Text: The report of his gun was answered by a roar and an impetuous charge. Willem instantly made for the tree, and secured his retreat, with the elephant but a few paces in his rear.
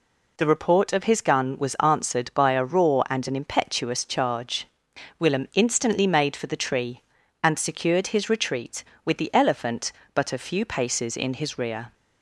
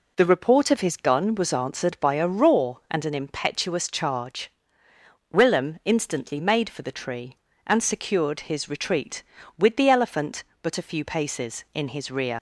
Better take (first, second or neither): first